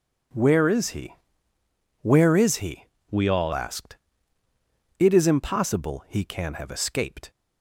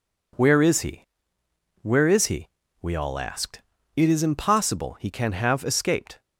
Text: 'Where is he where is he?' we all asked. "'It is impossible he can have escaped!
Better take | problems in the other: second | pauses between "he" and "where"; noticeable; at 1.1 s; 0.88 s long; noticeable in the second // changes voice from "we" to "all"; from 3.1 to 3.5 s; 0.4 s long

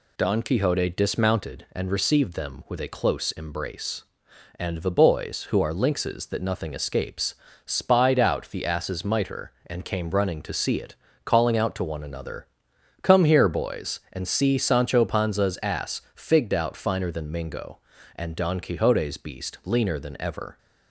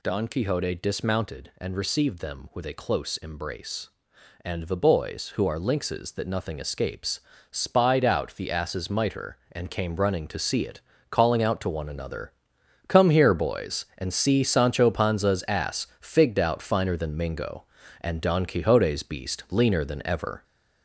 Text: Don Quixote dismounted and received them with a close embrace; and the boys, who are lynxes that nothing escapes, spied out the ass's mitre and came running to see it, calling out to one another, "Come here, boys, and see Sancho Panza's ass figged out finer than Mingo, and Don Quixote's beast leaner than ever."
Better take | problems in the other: first | gets louder; noticeable; throughout; 5 dB // pauses between "ass" and "figged"; slight; at 15.8 s; 0.16 s long; slight in the first

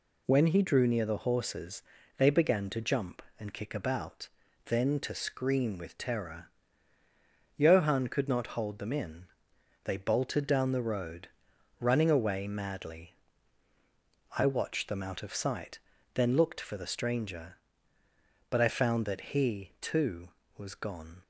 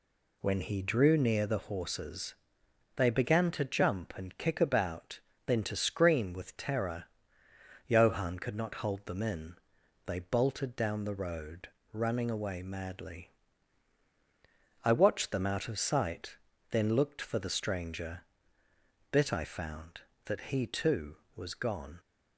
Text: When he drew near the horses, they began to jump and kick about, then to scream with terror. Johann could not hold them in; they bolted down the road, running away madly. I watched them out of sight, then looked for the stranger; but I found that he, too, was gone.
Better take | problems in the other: first | says "bit" for "but"; at 19.1 s

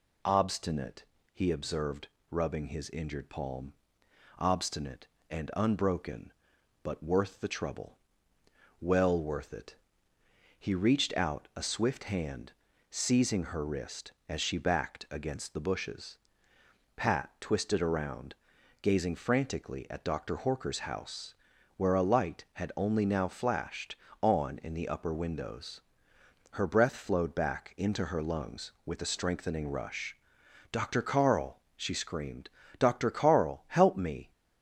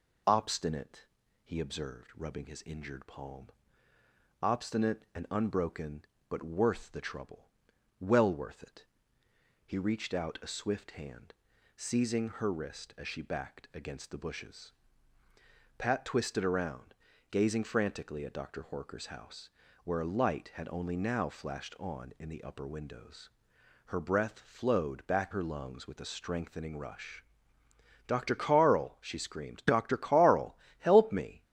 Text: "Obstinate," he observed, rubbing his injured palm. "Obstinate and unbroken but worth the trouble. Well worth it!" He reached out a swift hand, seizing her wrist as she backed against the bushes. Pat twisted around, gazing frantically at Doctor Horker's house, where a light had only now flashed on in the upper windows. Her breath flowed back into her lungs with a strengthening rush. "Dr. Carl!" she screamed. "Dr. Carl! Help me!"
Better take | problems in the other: first | skips "into"; at 25.3 s

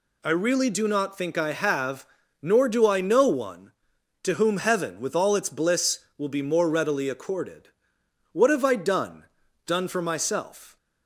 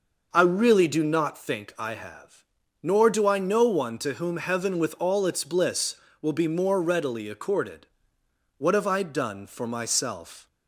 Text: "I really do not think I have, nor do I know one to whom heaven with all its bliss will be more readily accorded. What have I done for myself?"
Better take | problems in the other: second | says "done" twice; at 9.6 s

